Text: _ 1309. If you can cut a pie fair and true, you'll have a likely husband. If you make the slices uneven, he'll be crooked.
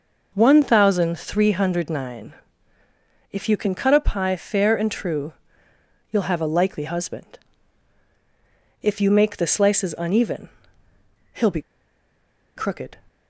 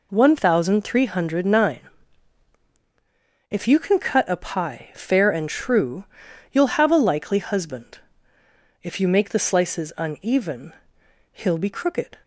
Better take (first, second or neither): second